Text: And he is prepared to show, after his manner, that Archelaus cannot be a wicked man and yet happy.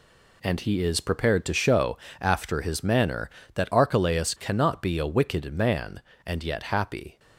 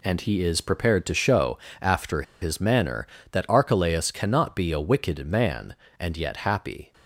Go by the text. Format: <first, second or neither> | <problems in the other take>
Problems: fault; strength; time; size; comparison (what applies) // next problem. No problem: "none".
first | pauses between "after" and "his"; slight; at 2.2 s; 0.19 s long